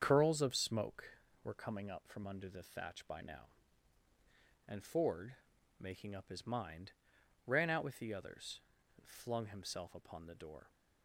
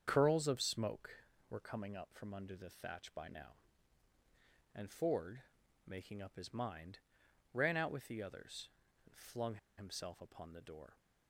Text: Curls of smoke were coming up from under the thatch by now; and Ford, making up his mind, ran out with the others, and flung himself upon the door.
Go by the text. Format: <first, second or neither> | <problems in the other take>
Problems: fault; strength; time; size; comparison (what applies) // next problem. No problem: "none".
first | starts louder than the rest; strong; until 1.0 s; 7.5 dB; strong in the first // pauses between "flung" and "himself"; slight; at 9.5 s; 0.20 s long